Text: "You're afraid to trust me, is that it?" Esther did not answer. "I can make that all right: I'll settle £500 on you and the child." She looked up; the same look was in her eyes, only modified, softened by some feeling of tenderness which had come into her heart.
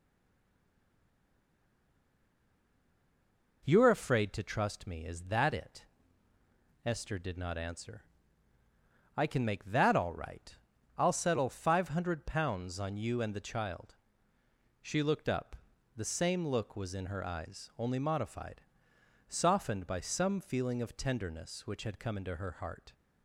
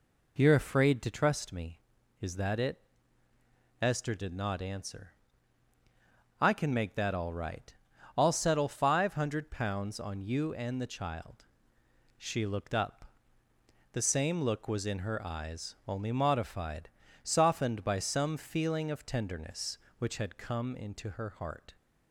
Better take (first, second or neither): second